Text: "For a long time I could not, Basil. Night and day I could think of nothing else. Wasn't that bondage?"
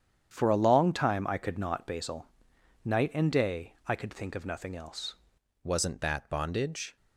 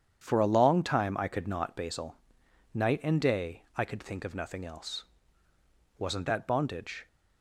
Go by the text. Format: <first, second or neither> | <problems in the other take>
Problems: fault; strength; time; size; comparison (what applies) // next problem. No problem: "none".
second | starts louder than the rest; strong; until 1.3 s; 9 dB; strong in the second // changes voice at "Wasn't"; from 5.6 s on; 1.3 s long